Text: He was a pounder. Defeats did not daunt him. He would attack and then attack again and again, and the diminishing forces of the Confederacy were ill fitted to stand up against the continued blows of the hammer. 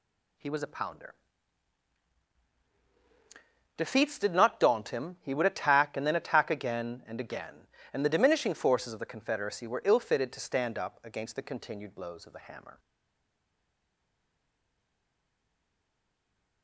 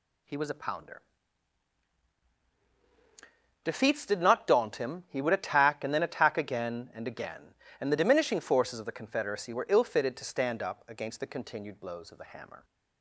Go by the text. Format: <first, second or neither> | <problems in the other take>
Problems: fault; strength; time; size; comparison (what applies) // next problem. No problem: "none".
second | stays silent after the last word; strong; from 12.7 s on; 3.9 s long